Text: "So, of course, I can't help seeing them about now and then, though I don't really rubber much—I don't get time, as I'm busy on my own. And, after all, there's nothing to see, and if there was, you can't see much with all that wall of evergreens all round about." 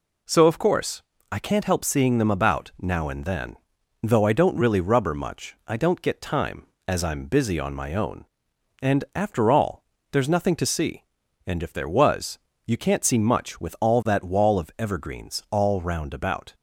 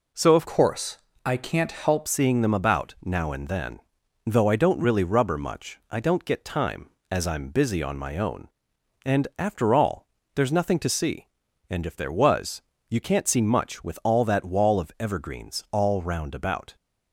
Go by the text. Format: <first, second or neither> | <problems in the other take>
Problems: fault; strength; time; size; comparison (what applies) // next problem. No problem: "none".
first | changes voice from "course" to "help"; from 0.4 to 2.0 s; 1.6 s long